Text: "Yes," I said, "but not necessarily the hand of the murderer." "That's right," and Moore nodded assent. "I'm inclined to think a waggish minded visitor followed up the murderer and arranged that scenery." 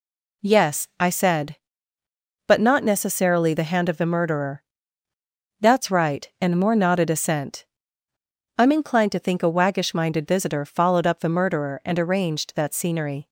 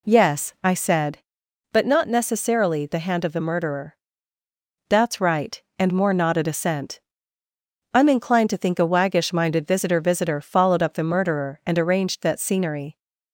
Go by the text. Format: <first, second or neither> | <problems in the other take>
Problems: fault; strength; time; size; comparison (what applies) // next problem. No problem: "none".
first | says "visitor" twice; at 10.0 s